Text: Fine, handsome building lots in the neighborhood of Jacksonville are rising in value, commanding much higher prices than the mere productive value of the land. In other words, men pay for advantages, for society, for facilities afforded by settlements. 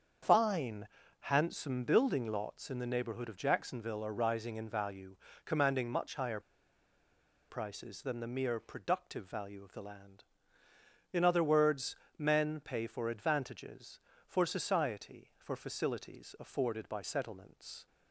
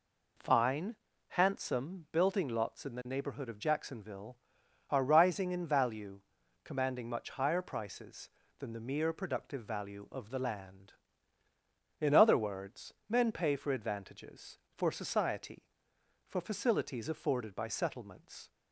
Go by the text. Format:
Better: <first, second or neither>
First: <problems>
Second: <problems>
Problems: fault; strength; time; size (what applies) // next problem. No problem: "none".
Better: second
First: starts louder than the rest; strong; until 1.5 s; 7 dB // pauses between "higher" and "prices"; at 6.3 s; 1.0 s long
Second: none